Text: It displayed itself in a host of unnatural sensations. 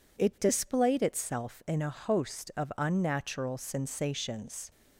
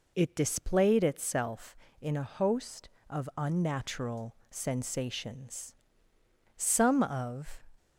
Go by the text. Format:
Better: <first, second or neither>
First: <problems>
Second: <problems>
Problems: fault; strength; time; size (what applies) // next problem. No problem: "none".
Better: first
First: none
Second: pauses between "unnatural" and "sensations"; slight; at 4.3 s; 0.16 s long // goes on to say "Some of"; noticeable; from 6.5 s on; 1.0 s long